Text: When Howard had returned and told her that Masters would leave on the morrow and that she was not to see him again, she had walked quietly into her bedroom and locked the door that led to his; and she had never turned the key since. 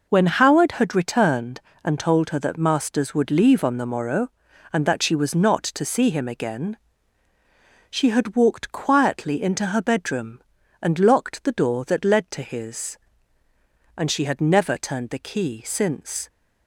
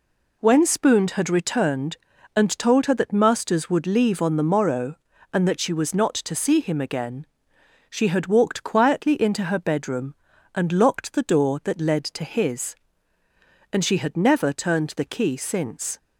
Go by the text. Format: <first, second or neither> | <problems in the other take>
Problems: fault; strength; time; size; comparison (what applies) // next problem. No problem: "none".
first | says "Spooned" for "Howard"; at 0.6 s